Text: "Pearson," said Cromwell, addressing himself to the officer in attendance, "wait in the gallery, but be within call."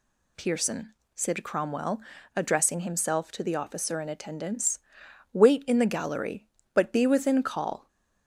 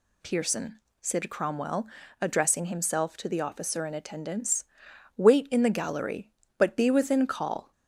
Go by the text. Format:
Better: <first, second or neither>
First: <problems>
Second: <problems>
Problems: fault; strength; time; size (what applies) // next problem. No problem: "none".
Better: neither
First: none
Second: none